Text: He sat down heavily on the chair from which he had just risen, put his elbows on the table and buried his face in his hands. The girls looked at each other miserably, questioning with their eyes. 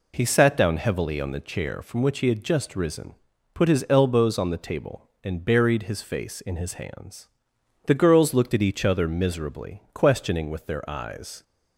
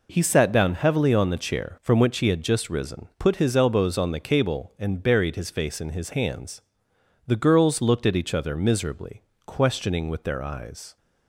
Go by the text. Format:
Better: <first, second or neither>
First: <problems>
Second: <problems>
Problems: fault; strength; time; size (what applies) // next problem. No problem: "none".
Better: first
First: none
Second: says "cable" for "table"; at 4.1 s